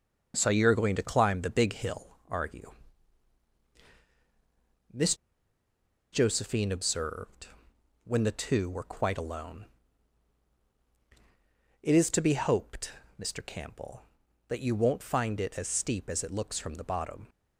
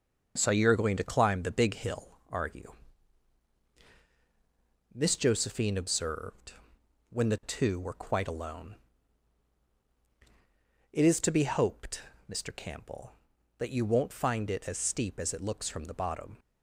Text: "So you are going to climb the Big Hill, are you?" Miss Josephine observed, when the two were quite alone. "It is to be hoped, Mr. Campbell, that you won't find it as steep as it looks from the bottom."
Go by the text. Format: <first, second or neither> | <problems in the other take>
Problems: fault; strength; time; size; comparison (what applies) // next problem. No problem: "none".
second | starts louder than the rest; until 1.3 s; 6.5 dB; also in the second // pauses between "Miss" and "Josephine"; noticeable; at 5.1 s; 0.97 s long